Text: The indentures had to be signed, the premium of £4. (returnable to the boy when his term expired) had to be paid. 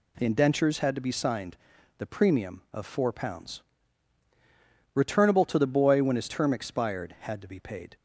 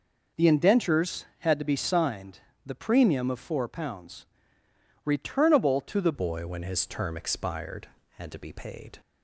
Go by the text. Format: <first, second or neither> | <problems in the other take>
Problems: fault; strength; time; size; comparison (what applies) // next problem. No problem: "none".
first | changes voice at "boy"; from 6.1 s on; 2.8 s long